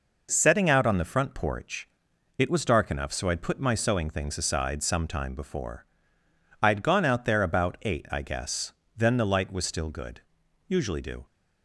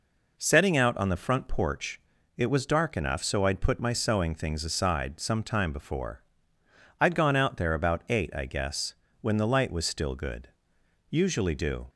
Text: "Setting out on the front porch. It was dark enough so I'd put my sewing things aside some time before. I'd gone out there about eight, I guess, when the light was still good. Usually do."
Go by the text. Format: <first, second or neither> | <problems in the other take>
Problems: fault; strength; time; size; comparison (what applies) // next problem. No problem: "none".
second | says "then" for "when"; at 8.9 s